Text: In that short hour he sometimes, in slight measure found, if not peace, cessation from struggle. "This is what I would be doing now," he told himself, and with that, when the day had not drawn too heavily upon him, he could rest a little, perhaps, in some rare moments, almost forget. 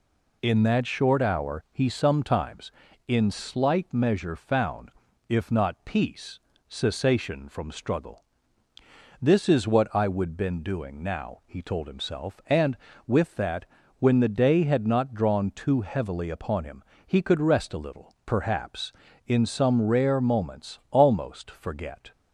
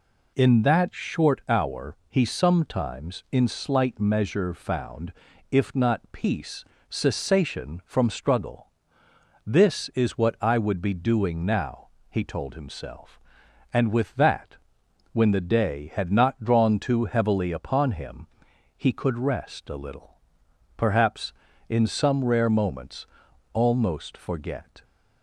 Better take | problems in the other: second | says "been" for "be"; at 10.3 s

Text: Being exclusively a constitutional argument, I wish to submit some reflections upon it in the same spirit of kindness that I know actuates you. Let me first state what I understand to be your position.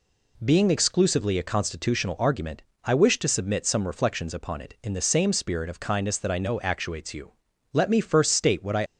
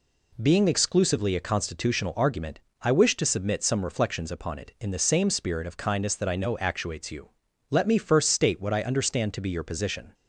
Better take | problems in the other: second | stops before "understand to be your position"; at 8.8 s

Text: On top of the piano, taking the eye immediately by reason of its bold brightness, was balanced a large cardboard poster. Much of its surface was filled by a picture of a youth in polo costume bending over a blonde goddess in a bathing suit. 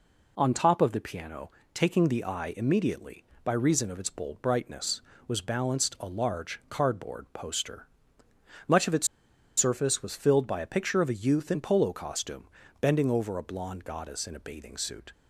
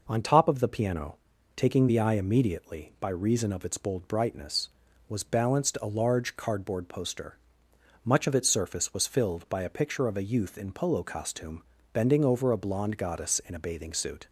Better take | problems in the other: second | pauses between "its" and "surface"; noticeable; at 9.0 s; 0.50 s long // pauses between "costume" and "bending"; slight; at 12.4 s; 0.34 s long; slight in the second

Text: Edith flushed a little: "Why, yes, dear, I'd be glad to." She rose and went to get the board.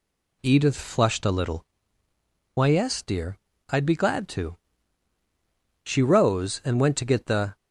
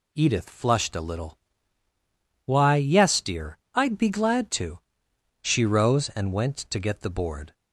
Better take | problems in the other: second | stops before "board"; at 7.5 s

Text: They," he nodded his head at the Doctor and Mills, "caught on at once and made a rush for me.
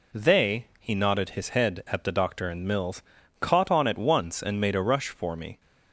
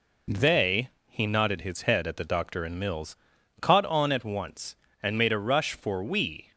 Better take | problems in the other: first | says "we" for "me"; at 6.0 s

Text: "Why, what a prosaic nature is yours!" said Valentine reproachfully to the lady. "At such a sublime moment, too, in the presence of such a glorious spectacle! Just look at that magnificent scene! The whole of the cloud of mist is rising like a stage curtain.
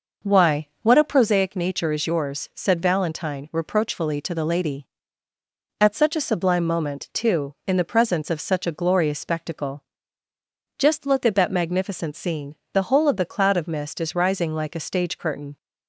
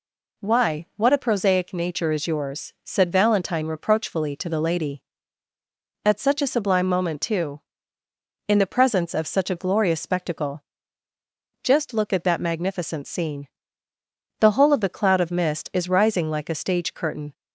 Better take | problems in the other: second | starts louder than the rest; noticeable; until 1.3 s; 5.5 dB

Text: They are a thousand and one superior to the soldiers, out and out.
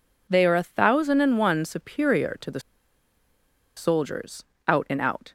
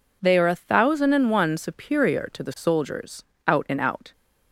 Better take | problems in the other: second | pauses between "the" and "soldiers"; at 2.5 s; 1.1 s long

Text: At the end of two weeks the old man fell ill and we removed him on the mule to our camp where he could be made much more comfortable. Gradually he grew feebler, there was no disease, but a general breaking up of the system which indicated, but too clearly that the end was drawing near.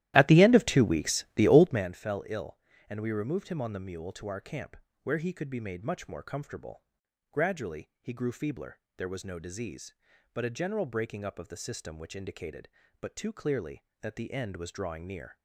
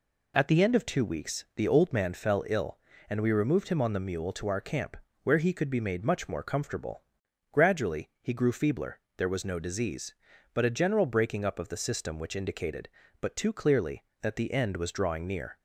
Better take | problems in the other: second | starts louder than the rest; strong; until 1.9 s; 14 dB // pauses between "camp" and "where"; slight; at 4.7 s; 0.26 s long; slight in the second

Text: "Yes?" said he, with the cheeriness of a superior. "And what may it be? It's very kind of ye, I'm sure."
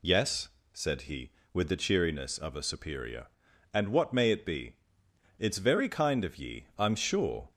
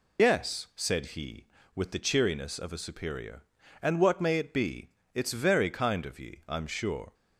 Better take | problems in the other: first | loses the start of "Yes"; at 0.1 s; 80 ms

